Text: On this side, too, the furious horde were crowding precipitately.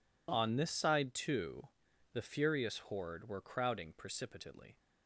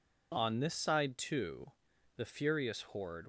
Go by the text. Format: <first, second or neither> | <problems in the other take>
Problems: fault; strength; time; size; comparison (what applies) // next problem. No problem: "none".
first | stops before "were crowding precipitately"; at 3.2 s